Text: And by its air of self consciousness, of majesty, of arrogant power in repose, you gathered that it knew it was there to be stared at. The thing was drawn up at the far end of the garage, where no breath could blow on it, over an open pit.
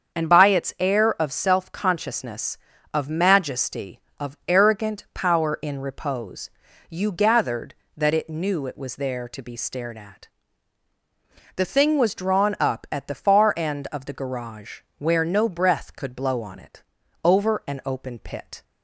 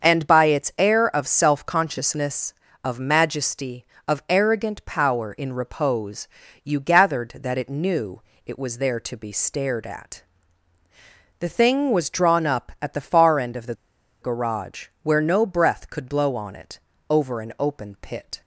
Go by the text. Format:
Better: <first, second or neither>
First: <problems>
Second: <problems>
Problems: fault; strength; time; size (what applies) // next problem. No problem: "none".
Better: first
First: starts louder than the rest; until 1.2 s; 7 dB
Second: starts louder than the rest; until 1.1 s; 6.5 dB // pauses between "knew" and "it"; slight; at 8.2 s; 0.24 s long // pauses between "the" and "garage"; noticeable; at 13.7 s; 0.46 s long